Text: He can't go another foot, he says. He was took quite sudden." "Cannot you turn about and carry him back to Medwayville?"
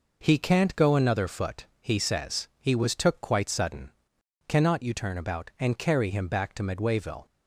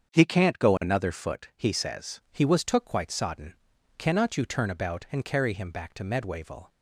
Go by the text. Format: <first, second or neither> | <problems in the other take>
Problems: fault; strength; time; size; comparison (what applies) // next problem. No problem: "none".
first | starts louder than the rest; strong; until 1.1 s; 7 dB // says "sodden" for "sudden"; at 3.1 s